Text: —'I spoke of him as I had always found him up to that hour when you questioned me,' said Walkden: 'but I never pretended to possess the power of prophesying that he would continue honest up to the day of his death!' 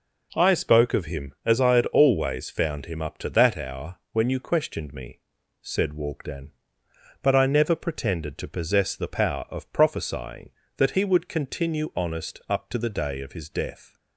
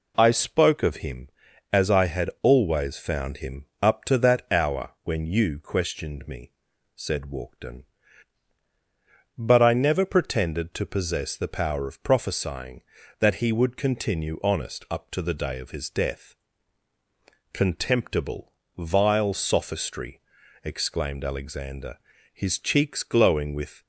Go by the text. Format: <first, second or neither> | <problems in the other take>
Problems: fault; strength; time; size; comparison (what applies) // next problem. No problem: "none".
first | pauses between "him" and "up"; slight; at 3.6 s; 0.16 s long // goes on to say "Contemptible vile sophistry exclaimed Alexander his cheeks glowing with"; strong; from 17.5 s on; 6.3 s long